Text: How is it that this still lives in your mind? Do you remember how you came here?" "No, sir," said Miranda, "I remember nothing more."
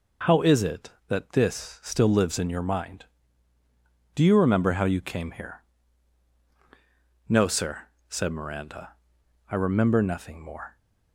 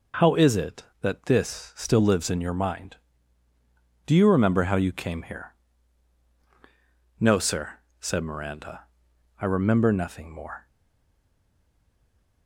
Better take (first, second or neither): first